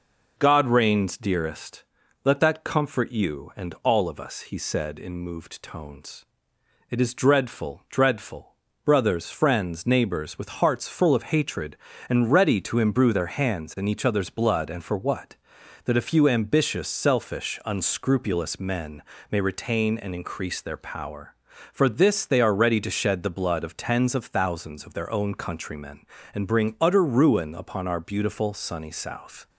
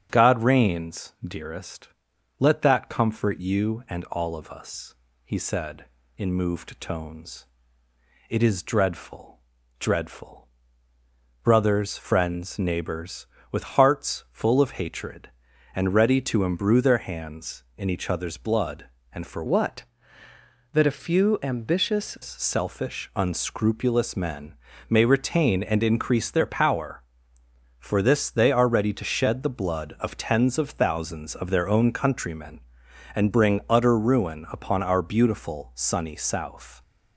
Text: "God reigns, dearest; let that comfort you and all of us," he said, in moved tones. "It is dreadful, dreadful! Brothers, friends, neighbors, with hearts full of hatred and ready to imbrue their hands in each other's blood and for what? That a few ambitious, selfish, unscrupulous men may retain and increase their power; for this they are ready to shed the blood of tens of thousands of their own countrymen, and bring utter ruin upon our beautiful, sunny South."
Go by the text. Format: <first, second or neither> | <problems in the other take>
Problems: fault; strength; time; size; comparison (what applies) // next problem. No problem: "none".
first | starts louder than the rest; strong; until 1.1 s; 8 dB // changes voice from "what" to "ambitious"; from 19.4 to 22.1 s; 2.7 s long // pauses between "men" and "may"; slight; at 24.5 s; 0.32 s long; slight in the first